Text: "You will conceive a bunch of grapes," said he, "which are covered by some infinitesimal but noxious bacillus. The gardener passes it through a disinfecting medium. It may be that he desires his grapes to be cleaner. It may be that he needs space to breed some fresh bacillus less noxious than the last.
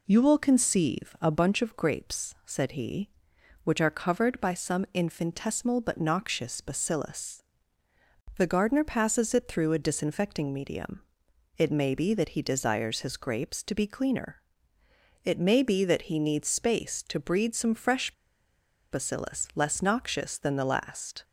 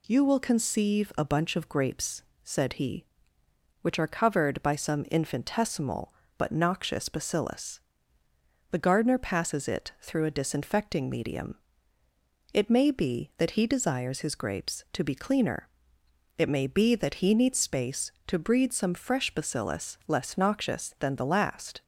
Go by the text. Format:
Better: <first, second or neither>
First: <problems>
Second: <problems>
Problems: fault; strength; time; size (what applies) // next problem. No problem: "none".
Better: second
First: pauses between "fresh" and "bacillus"; noticeable; at 18.1 s; 0.78 s long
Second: none